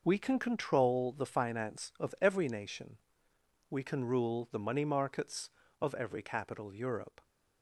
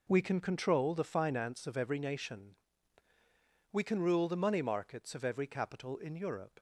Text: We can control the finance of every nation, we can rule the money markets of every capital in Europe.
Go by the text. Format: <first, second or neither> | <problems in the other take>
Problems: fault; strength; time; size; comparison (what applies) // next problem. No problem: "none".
second | skips "in"; at 6.7 s